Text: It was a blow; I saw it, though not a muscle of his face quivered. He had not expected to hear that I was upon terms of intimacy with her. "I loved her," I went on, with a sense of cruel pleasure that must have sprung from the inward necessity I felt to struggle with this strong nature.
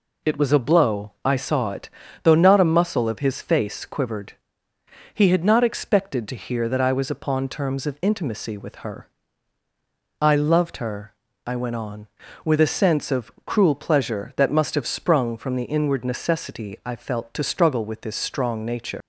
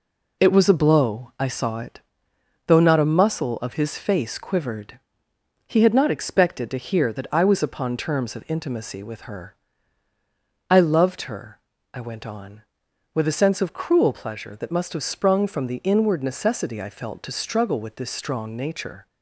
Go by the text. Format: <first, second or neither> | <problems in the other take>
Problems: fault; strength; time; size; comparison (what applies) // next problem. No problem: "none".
second | leaves "nature" unfinished; at 19.0 s; 125 ms